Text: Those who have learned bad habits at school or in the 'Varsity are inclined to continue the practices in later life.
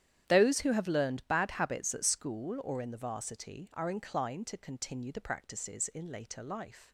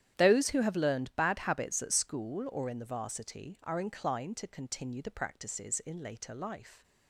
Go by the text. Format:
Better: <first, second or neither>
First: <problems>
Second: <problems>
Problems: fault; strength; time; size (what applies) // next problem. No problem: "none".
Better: neither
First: starts louder than the rest; strong; until 1.3 s; 10.5 dB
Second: starts louder than the rest; strong; until 1.2 s; 10.5 dB